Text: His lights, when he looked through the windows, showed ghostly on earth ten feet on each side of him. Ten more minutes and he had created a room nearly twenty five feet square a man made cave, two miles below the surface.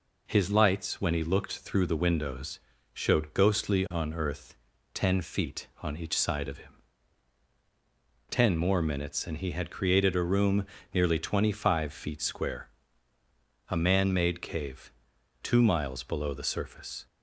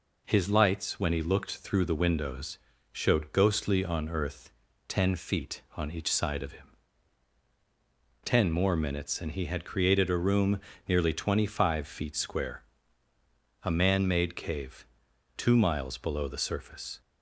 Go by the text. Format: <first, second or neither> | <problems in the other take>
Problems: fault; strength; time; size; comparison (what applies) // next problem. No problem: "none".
neither | pauses between "earth" and "ten"; the same in both // pauses between "room" and "nearly"; slight; the same in both // pauses between "square" and "a"; the same in both